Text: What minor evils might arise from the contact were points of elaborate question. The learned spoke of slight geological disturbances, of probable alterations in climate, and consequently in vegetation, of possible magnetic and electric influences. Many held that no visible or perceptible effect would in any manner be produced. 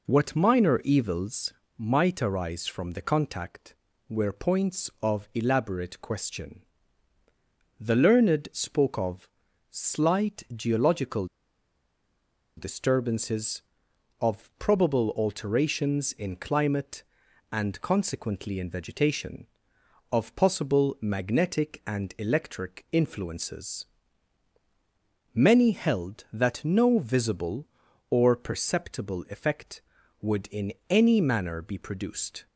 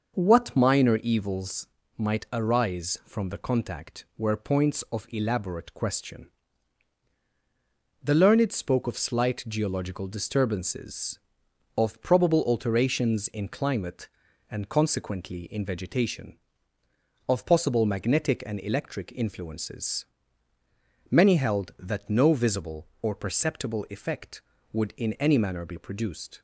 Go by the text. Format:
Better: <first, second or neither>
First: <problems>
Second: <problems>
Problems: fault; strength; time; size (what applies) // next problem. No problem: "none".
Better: second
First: pauses between "evils" and "might"; slight; at 1.5 s; 0.28 s long // pauses between "of" and "slight"; at 9.2 s; 0.44 s long // pauses between "geological" and "disturbances"; strong; at 11.2 s; 1.3 s long // pauses between "in" and "any"; slight; at 30.7 s; 0.16 s long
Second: pauses between "evils" and "might"; slight; at 1.6 s; 0.32 s long